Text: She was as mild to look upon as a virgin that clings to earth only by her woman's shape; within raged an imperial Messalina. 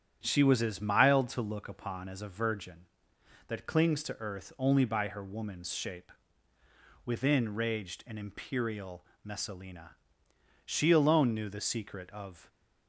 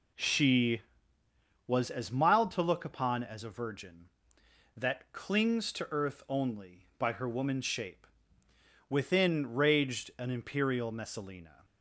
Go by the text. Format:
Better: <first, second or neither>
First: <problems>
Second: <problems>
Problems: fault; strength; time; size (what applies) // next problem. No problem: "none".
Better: second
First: starts louder than the rest; strong; until 1.2 s; 9.5 dB // pauses between "imperial" and "Messalina"; slight; at 9.0 s; 0.20 s long // goes on to say "She alone knew the secret of"; strong; from 10.6 s on; 1.8 s long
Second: none